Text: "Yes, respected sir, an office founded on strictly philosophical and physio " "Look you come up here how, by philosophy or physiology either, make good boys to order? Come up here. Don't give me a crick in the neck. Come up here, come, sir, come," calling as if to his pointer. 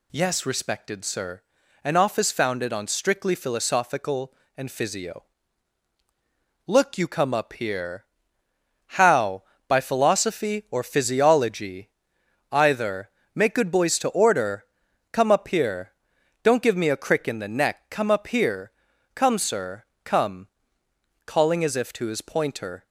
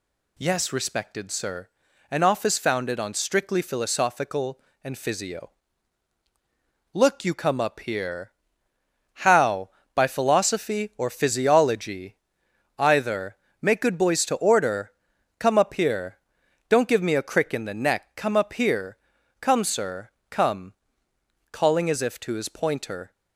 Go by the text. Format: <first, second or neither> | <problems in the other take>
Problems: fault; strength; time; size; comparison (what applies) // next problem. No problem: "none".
neither | pauses between "here" and "how"; noticeable; the same in both // pauses between "physiology" and "either"; noticeable; the same in both